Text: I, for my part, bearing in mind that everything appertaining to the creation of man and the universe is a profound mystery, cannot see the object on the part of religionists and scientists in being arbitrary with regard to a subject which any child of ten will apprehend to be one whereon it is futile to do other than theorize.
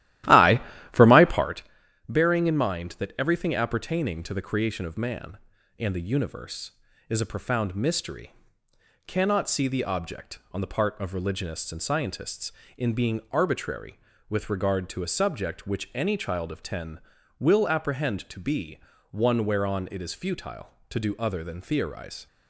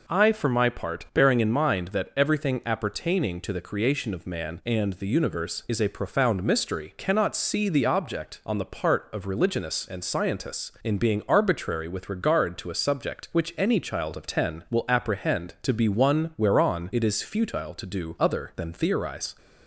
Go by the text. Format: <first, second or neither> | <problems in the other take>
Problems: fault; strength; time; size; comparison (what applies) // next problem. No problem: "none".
second | starts louder than the rest; strong; until 1.6 s; 14.5 dB // pauses between "be" and "one"; slight; at 18.7 s; 0.32 s long